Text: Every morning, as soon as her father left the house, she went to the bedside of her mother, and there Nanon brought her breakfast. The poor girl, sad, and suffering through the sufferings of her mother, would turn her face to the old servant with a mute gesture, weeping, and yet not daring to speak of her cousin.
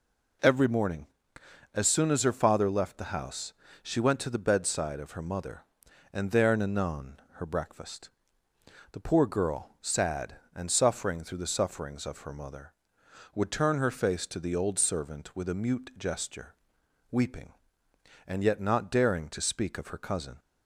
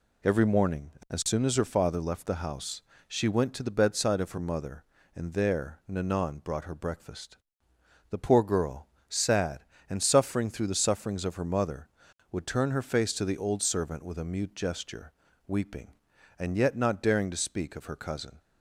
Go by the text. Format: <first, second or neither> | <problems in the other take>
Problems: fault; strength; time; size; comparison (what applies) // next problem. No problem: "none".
second | skips "brought"; at 7.2 s